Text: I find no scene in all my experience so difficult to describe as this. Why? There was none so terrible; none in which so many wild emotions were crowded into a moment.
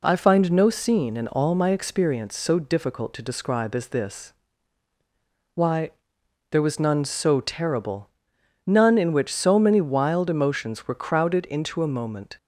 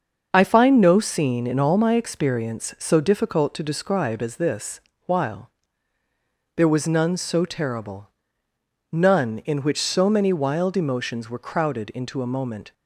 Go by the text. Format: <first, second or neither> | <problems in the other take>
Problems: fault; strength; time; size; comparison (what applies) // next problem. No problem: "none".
first | starts louder than the rest; until 1.3 s; 6.5 dB // says "While" for "Why"; at 5.0 s